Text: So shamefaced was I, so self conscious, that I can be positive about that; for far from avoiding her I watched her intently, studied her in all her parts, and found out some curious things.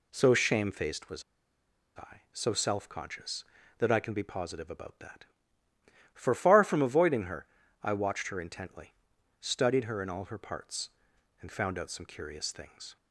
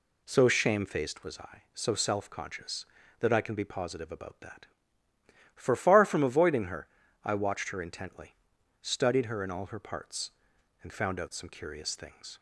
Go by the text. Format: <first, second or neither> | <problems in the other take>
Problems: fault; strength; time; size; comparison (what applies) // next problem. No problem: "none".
second | pauses between "was" and "I"; noticeable; at 1.2 s; 0.73 s long // pauses between "her" and "I"; at 7.4 s; 0.38 s long; also in the second